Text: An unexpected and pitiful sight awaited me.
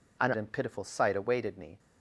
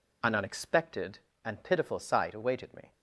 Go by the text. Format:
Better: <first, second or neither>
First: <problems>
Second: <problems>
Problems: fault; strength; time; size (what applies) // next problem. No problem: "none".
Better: second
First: skips "unexpected"; at 0.3 s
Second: none